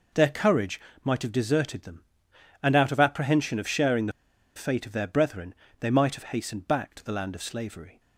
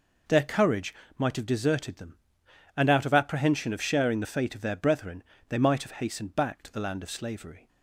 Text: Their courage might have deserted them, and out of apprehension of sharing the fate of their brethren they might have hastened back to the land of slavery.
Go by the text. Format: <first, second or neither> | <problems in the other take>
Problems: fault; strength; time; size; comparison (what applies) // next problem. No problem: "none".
second | pauses between "courage" and "might"; slight; at 0.7 s; 0.26 s long; slight in the second // pauses between "the" and "fate"; at 4.1 s; 0.44 s long // pauses between "brethren" and "they"; slight; at 5.5 s; 0.26 s long; slight in the second